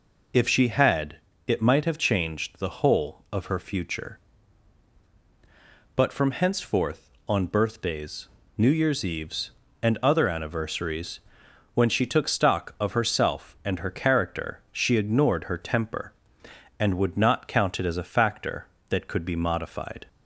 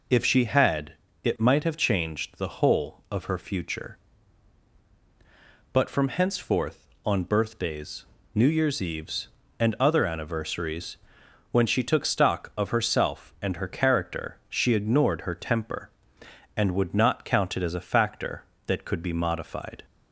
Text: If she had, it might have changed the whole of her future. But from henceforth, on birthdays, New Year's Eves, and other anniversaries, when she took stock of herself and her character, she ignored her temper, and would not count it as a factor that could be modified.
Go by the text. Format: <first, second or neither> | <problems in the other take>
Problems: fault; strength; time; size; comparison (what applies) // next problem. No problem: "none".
neither | none